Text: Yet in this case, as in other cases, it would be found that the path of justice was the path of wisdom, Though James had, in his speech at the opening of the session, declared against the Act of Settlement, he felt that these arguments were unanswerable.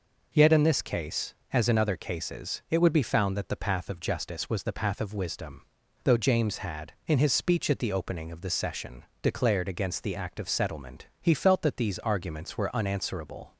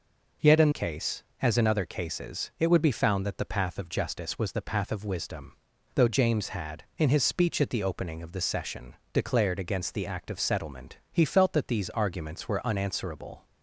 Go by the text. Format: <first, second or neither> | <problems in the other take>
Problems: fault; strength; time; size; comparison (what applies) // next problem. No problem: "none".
first | skips "this"; at 0.7 s